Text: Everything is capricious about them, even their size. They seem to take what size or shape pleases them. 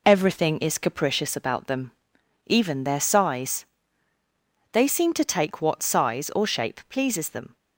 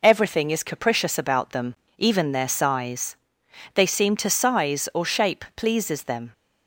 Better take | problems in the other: first | skips "take what"; at 4.3 s

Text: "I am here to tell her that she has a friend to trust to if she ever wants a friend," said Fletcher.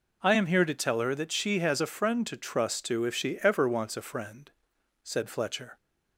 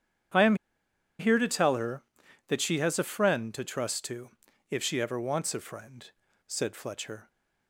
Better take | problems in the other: first | starts louder than the rest; strong; until 2.0 s; 9.5 dB // pauses between "am" and "here"; noticeable; at 0.5 s; 0.64 s long // pauses between "to" and "if"; at 4.3 s; 0.40 s long

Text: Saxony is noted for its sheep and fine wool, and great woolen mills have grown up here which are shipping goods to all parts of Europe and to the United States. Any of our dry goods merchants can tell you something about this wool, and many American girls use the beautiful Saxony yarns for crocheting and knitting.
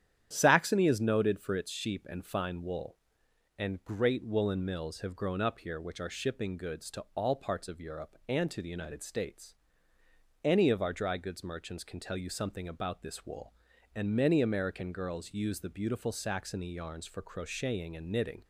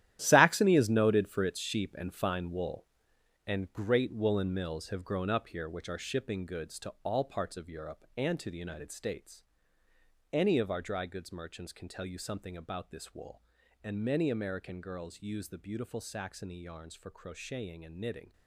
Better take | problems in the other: first | gets quieter; strong; throughout; 11.5 dB // starts louder than the rest; strong; until 1.2 s; 12 dB; strong in the first

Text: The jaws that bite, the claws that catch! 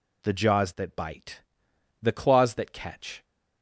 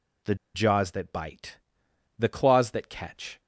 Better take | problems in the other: first | pauses between "The" and "jaws"; slight; at 0.3 s; 0.19 s long

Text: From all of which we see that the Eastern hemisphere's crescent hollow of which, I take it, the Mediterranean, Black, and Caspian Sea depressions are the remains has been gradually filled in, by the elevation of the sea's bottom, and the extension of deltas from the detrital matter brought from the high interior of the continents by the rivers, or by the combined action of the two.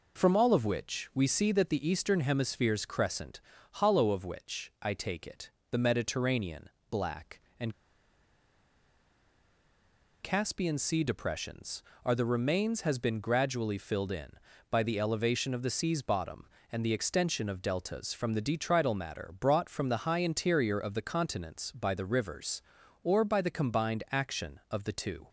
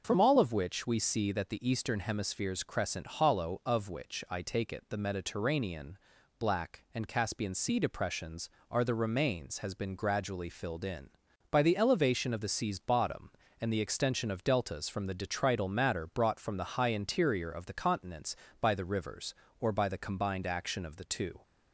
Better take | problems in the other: second | pauses between "crescent" and "hollow"; slight; at 3.3 s; 0.34 s long // pauses between "and" and "Caspian"; strong; at 7.7 s; 2.4 s long

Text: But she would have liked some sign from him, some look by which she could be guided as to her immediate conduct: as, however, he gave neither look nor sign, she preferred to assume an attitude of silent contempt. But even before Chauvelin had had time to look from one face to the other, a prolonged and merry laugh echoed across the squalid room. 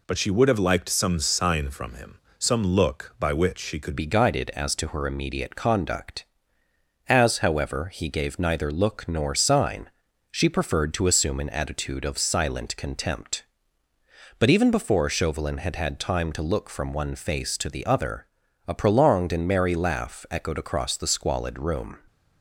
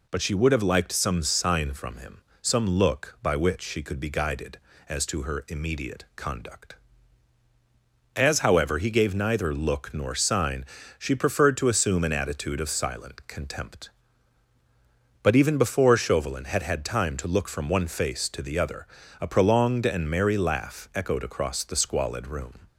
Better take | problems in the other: second | changes voice at "be"; from 3.9 s on; 18.0 s long

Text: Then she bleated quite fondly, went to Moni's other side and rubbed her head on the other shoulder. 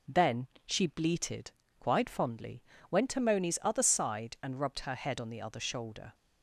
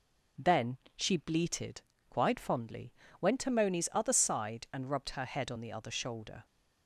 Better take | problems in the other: neither | pauses between "Then" and "she"; slight; the same in both // pauses between "bleated" and "quite"; slight; the same in both

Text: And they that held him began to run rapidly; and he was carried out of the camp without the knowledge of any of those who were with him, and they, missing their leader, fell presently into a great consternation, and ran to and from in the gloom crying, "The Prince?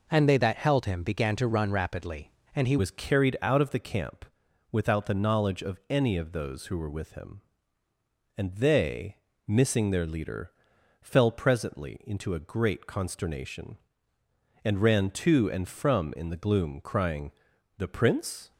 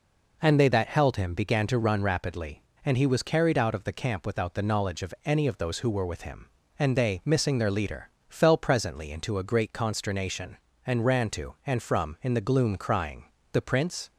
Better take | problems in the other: second | changes voice at "was"; from 2.7 s on; 15.8 s long // pauses between "camp" and "without"; noticeable; at 4.2 s; 0.46 s long

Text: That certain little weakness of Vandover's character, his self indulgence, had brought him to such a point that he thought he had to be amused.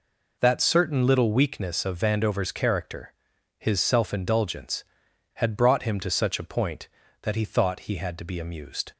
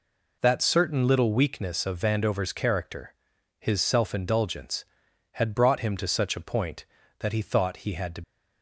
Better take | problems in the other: first | stops before "be amused"; at 8.2 s

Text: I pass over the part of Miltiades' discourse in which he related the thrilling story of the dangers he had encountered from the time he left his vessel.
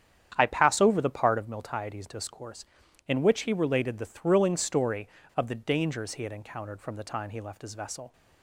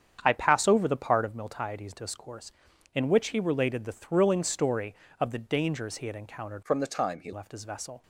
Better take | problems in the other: first | starts louder than the rest; strong; until 1.2 s; 8.5 dB; strong in the first // changes voice from "from" to "he"; from 6.6 to 7.3 s; 0.7 s long

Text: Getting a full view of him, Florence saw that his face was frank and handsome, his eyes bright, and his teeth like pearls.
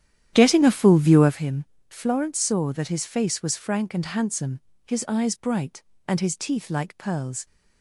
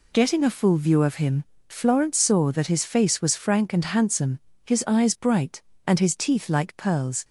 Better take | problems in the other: second | starts louder than the rest; strong; until 1.4 s; 10.5 dB

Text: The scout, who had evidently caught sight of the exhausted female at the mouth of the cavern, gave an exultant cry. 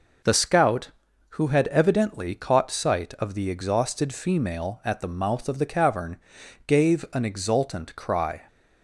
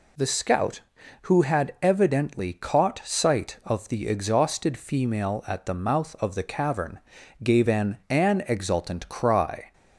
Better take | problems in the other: first | says "an" twice; at 8.0 s

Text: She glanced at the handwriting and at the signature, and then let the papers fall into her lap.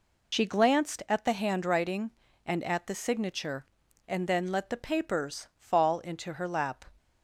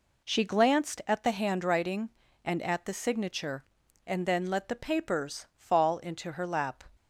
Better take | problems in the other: second | loses the start of "She"; at 0.3 s; 60 ms

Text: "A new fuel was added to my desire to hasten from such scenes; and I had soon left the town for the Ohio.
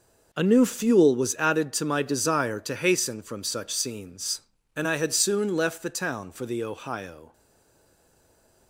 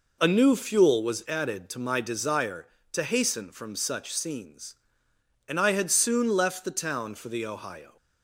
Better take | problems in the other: second | stays silent after the last word; noticeable; from 7.3 s on; 1.3 s long

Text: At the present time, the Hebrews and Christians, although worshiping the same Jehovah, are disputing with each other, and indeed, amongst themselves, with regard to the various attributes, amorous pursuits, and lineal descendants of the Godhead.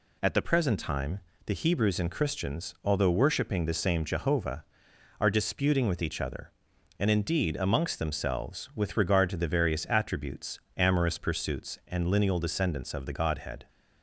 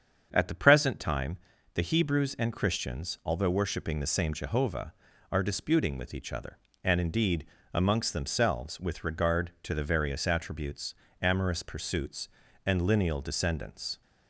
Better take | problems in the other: first | starts louder than the rest; strong; until 1.3 s; 7.5 dB // stops before "of the Godhead"; at 14.0 s

